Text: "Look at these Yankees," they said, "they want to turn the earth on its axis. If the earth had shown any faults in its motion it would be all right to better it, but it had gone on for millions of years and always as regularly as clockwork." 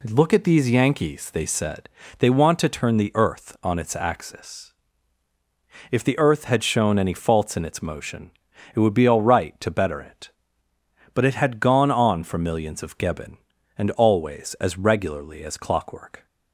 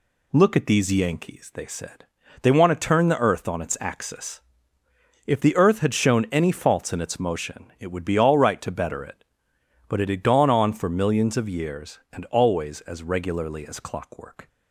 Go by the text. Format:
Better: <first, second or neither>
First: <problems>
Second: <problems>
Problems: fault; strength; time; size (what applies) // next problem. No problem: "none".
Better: second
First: pauses between "motion" and "it"; at 8.3 s; 0.42 s long // says "geben" for "years"; at 12.9 s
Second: none